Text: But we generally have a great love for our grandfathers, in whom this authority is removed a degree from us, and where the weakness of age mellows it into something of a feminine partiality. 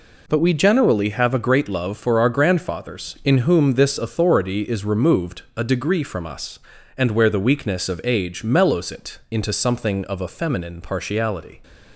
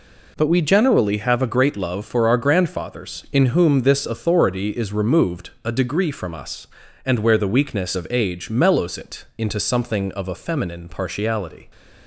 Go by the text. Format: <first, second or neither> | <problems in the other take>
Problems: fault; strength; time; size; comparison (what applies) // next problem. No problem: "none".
neither | none